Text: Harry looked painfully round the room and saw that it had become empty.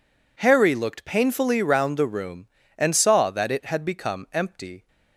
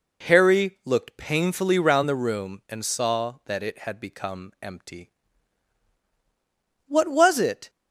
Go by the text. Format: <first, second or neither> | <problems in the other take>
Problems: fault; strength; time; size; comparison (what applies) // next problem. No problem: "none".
first | goes on to say "What was it"; noticeable; from 6.8 s on; 0.82 s long